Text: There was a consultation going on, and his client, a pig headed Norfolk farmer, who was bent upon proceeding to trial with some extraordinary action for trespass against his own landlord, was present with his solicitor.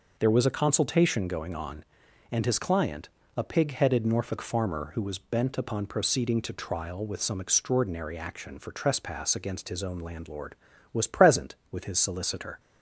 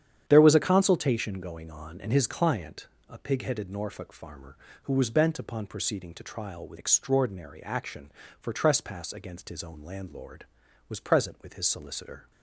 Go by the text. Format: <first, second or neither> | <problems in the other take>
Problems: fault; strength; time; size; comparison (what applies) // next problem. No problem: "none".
first | starts louder than the rest; strong; until 1.2 s; 9 dB // skips "some"; at 6.7 s